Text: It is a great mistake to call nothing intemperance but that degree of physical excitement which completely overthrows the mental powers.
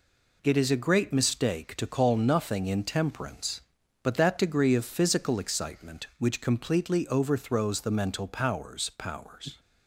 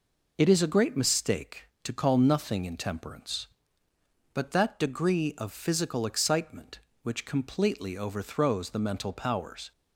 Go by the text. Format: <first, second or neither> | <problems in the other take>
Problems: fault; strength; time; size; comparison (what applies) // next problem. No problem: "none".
second | says "powers" twice; at 8.9 s